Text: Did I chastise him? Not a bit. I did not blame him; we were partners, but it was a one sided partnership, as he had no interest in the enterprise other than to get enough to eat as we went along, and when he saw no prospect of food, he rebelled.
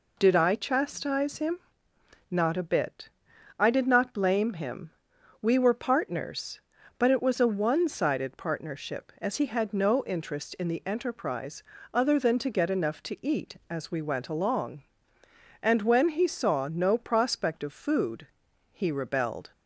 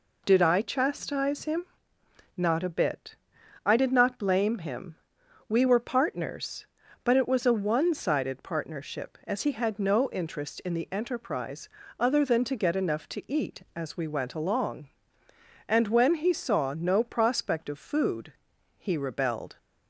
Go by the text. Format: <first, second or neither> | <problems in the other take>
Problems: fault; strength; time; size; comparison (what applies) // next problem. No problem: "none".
neither | pauses between "enterprise" and "other"; slight; the same in both